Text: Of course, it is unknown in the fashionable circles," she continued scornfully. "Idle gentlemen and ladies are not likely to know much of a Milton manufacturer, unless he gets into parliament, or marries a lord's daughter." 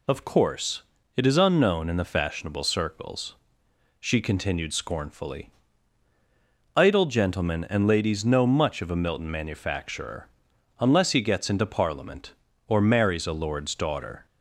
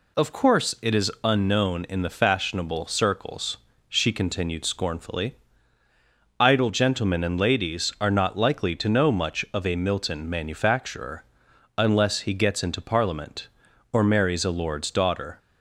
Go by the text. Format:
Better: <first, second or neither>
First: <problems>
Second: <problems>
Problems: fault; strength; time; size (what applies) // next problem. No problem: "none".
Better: second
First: skips "are not likely to"; at 8.2 s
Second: none